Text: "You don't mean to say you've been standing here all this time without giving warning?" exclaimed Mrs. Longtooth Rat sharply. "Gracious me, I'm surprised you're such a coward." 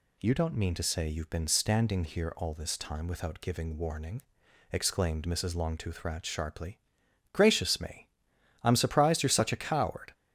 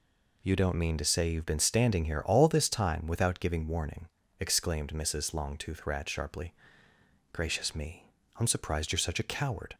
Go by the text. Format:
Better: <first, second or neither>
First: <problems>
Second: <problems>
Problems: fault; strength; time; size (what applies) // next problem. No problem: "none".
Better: neither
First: none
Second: none